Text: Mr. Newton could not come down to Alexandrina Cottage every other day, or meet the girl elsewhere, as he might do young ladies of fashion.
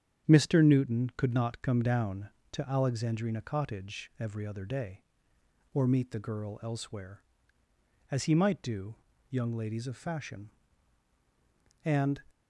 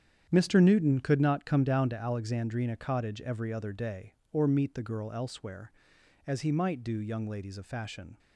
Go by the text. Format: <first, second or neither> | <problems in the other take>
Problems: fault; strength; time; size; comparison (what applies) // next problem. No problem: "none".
second | starts louder than the rest; strong; until 1.3 s; 8.5 dB; strong in the second // pauses between "do" and "young"; slight; at 8.9 s; 0.36 s long // goes on to say "And"; slight; from 11.8 s on; 0.38 s long